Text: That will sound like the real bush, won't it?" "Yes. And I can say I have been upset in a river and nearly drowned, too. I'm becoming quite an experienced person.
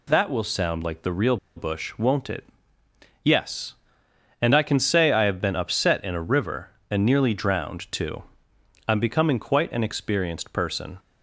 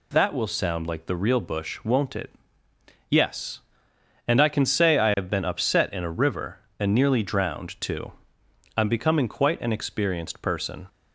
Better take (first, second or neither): second